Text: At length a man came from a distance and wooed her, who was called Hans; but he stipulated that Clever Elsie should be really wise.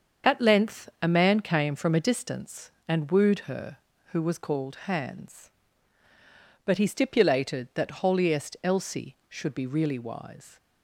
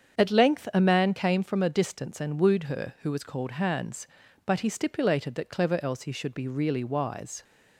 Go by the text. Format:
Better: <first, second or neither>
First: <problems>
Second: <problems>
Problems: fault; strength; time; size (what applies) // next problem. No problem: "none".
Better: second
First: starts louder than the rest; until 1.3 s; 7 dB // says "Holiest" for "Clever"; at 8.0 s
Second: starts louder than the rest; strong; until 1.2 s; 7.5 dB